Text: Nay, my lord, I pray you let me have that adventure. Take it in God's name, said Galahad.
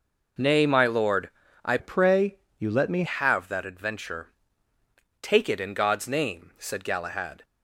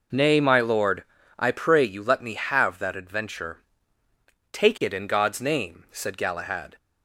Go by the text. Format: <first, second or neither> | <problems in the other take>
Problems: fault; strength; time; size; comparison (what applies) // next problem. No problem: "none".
second | changes voice from "pray" to "me"; from 1.7 to 3.0 s; 1.3 s long // pauses between "pray" and "you"; slight; at 2.3 s; 0.20 s long